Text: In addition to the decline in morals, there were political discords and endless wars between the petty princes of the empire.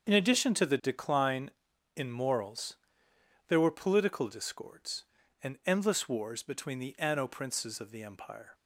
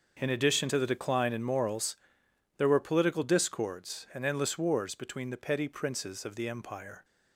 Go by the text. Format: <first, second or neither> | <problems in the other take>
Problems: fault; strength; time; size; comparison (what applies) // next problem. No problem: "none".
second | starts louder than the rest; until 1.1 s; 7 dB; also in the second // says "anno" for "petty"; at 6.9 s